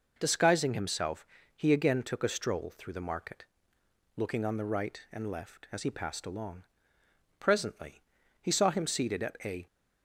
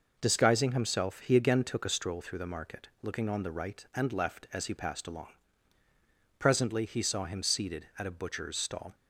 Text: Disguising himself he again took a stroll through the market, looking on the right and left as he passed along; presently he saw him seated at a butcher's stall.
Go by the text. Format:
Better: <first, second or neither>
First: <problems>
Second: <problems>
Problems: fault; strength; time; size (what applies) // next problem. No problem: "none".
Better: second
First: pauses between "himself" and "he"; slight; at 1.2 s; 0.28 s long // pauses between "presently" and "he"; at 8.0 s; 0.40 s long // stops before "butcher's stall"; at 9.6 s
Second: none